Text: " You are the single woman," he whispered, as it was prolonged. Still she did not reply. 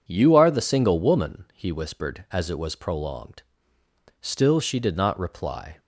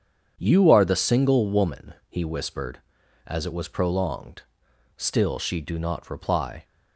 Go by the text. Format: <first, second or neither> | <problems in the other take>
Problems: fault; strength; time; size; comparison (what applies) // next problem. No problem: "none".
first | starts louder than the rest; strong; until 1.3 s; 7.5 dB // says "do" for "did"; at 5.6 s